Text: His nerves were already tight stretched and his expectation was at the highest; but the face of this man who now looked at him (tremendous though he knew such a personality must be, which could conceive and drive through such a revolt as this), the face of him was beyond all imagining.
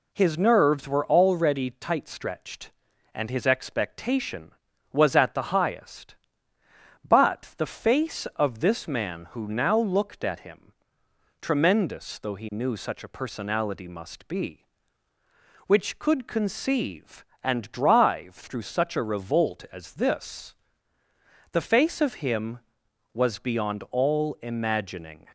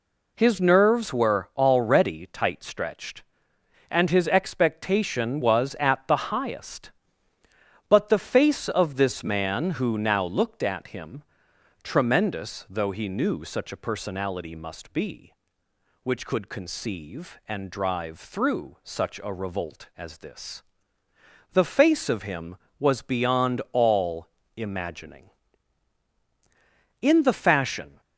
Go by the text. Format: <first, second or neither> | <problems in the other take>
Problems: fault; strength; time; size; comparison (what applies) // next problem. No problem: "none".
first | pauses between "the" and "highest"; slight; at 6.1 s; 0.16 s long // goes on to say "In the fashion"; noticeable; from 27.0 s on; 0.98 s long